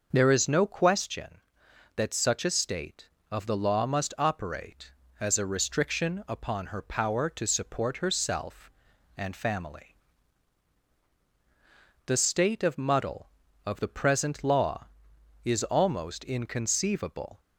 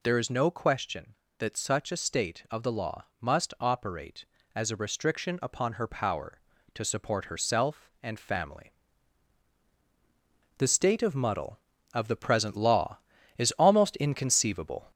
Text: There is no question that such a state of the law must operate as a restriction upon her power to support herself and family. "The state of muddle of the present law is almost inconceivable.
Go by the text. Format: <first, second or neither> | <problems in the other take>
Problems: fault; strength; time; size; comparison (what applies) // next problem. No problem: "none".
first | gets louder; slight; throughout; 2.5 dB